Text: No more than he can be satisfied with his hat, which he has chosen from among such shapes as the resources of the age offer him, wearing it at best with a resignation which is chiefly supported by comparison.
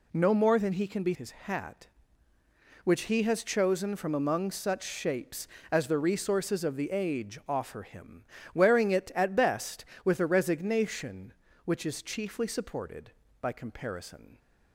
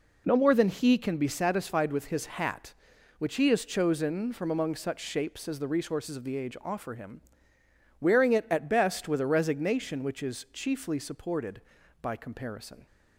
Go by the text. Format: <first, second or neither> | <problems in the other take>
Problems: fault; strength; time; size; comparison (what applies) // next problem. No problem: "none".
second | skips "satisfied with"; at 1.1 s